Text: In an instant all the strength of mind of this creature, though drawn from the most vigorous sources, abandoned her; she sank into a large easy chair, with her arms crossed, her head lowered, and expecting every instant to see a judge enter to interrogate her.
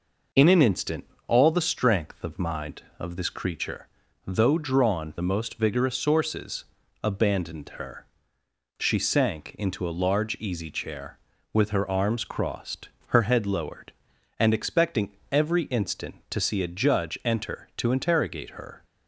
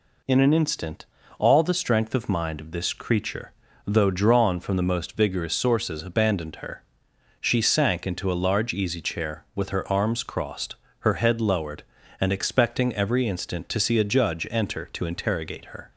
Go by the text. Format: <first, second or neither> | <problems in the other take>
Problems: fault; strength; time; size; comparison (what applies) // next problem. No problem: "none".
second | pauses between "instant" and "all"; slight; at 1.0 s; 0.24 s long; slight in the second // skips "from"; at 5.1 s // pauses between "expecting" and "every"; slight; at 15.1 s; 0.22 s long